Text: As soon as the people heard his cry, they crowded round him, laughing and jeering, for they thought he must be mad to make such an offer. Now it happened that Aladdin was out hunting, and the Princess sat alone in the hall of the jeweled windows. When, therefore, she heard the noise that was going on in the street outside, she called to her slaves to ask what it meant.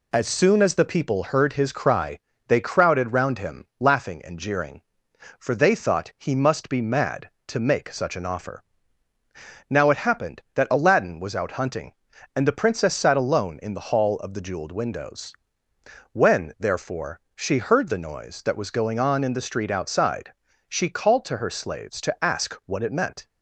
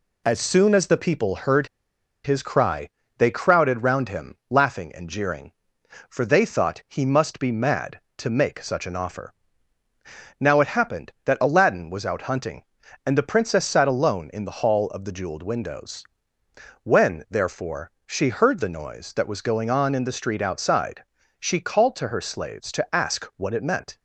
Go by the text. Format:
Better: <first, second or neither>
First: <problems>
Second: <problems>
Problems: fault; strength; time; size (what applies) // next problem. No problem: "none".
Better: first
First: none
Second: pauses between "heard" and "his"; noticeable; at 1.6 s; 0.58 s long